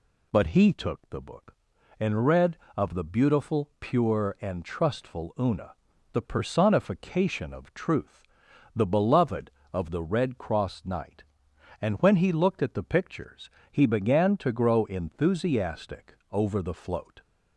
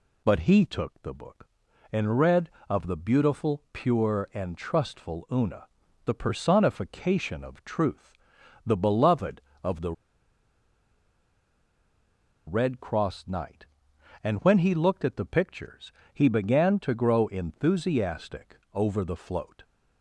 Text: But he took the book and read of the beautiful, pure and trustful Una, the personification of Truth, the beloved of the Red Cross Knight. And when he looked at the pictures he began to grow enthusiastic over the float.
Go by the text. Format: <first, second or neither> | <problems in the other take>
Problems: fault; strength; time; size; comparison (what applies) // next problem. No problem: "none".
first | pauses between "the" and "Red"; strong; at 9.9 s; 2.5 s long // pauses between "pictures" and "he"; slight; at 15.9 s; 0.22 s long; slight in the first // pauses between "enthusiastic" and "over"; slight; at 18.5 s; 0.16 s long; slight in the first